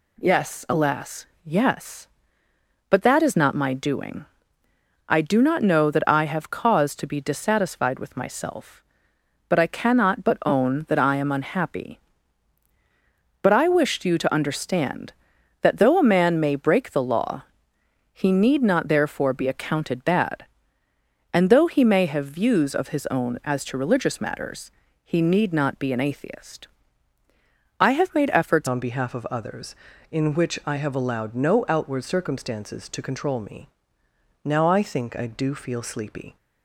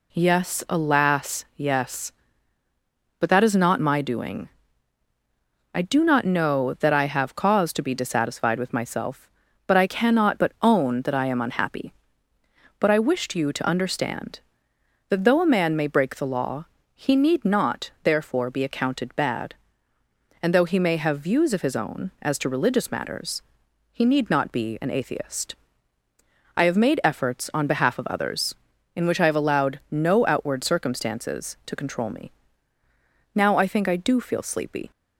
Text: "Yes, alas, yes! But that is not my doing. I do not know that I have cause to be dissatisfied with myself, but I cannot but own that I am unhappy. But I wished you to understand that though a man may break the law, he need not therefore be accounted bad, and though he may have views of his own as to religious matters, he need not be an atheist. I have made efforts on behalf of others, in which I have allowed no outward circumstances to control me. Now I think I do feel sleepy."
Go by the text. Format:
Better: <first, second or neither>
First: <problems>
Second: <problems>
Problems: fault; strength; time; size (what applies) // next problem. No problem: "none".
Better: second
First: changes voice at "on"; from 28.6 s on; 7.7 s long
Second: none